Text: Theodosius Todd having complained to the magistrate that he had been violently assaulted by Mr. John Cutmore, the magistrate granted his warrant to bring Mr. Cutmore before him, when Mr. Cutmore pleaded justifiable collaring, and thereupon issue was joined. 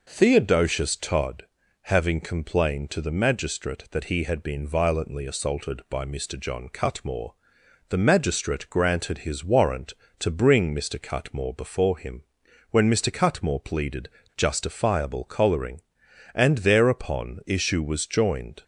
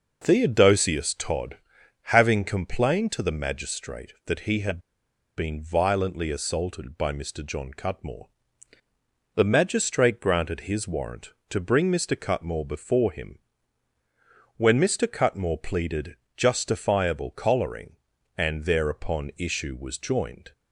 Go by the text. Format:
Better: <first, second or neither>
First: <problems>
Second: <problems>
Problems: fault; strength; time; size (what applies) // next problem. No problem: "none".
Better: first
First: pauses between "Todd" and "having"; at 1.4 s; 0.38 s long // pauses between "pleaded" and "justifiable"; slight; at 14.0 s; 0.27 s long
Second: pauses between "Todd" and "having"; noticeable; at 1.5 s; 0.60 s long // pauses between "had" and "been"; noticeable; at 4.7 s; 0.58 s long // pauses between "pleaded" and "justifiable"; slight; at 16.1 s; 0.22 s long